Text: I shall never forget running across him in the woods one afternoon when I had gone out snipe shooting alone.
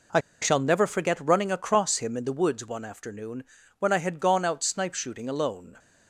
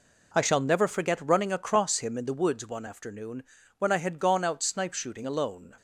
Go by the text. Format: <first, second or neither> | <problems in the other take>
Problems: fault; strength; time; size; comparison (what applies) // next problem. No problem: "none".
second | pauses between "I" and "shall"; slight; at 0.1 s; 0.22 s long // pauses between "afternoon" and "when"; slight; at 3.4 s; 0.36 s long; slight in the second